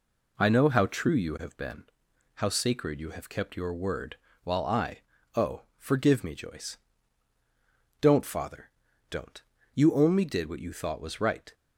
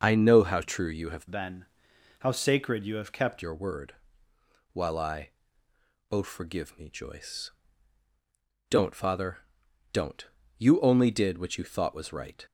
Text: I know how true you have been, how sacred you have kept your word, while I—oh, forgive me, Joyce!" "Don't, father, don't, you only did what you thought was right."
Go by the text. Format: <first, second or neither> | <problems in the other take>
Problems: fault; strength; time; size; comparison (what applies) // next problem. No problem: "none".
first | starts louder than the rest; until 1.0 s; 6 dB // changes voice from "been" to "kept"; from 1.2 to 3.4 s; 2.2 s long